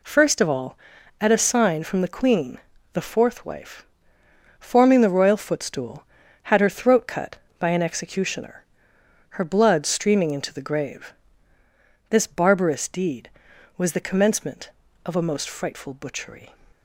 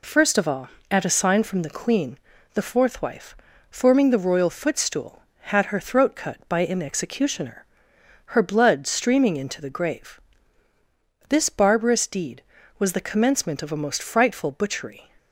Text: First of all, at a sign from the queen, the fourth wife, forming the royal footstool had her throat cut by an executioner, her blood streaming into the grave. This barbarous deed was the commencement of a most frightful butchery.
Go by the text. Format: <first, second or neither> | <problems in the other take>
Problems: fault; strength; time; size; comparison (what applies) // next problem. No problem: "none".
neither | none